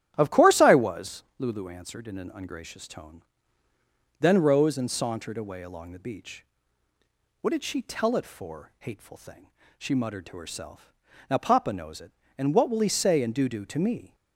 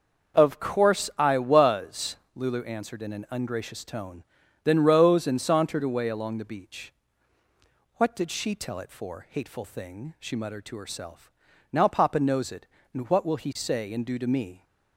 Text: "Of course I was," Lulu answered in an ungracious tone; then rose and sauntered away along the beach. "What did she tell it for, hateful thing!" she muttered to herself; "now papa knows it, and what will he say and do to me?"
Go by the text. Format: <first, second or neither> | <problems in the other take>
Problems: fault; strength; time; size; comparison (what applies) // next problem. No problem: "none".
second | starts louder than the rest; strong; until 1.1 s; 11 dB; also in the second // says "do" twice; at 13.4 s